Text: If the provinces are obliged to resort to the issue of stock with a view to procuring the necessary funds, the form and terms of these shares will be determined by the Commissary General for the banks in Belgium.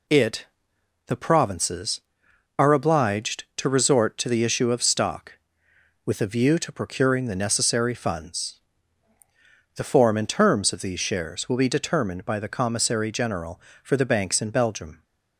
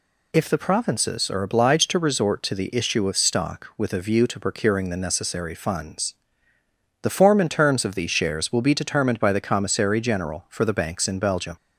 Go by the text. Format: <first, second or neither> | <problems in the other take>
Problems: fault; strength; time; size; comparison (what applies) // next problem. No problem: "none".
second | says "It" for "If"; at 0.0 s